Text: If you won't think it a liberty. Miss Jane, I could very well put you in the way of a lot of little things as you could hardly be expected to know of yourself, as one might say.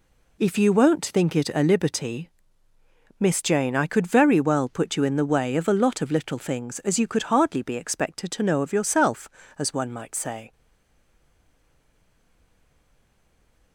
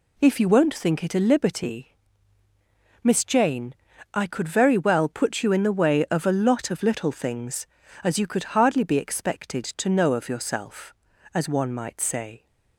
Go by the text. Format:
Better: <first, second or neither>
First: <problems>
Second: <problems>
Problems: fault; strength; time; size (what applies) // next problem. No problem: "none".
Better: second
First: stays silent after the last word; strong; from 10.5 s on; 3.2 s long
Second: none